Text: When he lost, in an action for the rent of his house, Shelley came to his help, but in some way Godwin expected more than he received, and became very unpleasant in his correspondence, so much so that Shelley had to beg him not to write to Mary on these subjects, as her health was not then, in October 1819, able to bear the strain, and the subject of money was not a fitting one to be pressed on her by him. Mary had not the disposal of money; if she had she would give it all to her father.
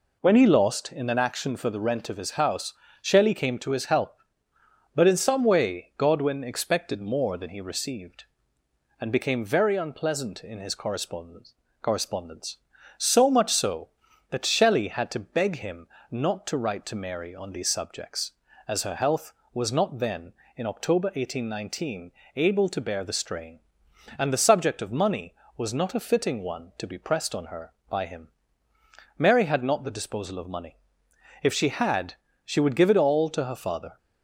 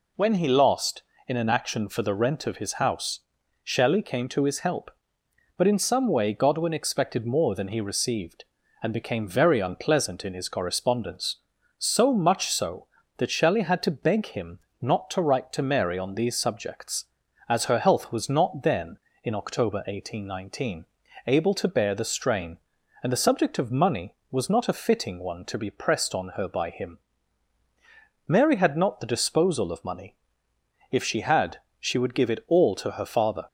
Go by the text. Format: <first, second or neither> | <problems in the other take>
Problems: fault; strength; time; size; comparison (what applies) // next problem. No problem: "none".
second | says "correspondence" twice; at 11.8 s // pauses between "him" and "not"; slight; at 15.8 s; 0.24 s long; slight in the second // pauses between "had" and "she"; slight; at 32.1 s; 0.30 s long; slight in the second